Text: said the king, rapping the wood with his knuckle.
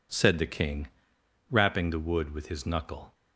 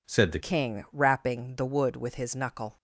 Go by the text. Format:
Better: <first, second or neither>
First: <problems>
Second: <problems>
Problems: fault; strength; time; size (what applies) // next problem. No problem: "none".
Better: first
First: none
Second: changes voice at "king"; from 0.3 s on; 2.4 s long